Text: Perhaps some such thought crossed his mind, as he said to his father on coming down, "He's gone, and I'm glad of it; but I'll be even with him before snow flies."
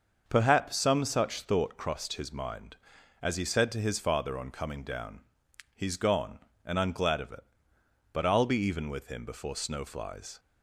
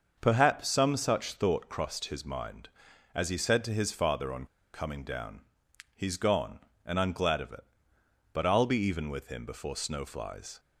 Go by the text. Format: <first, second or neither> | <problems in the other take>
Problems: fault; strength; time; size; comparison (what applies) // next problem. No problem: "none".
first | starts louder than the rest; until 1.2 s; 6.5 dB; also in the first // pauses between "on" and "coming"; slight; at 4.4 s; 0.27 s long